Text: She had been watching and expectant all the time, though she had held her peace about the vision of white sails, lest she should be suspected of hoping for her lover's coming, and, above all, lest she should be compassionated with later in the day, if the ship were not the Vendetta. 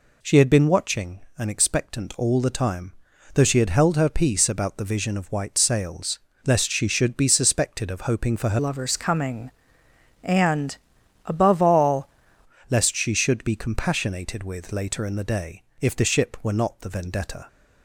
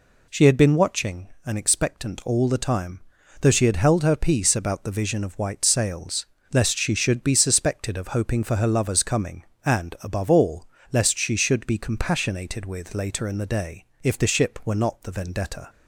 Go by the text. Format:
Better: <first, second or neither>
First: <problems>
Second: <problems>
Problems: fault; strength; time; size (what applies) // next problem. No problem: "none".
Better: second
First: changes voice from "lover's" to "all"; from 8.5 to 12.0 s; 3.5 s long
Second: none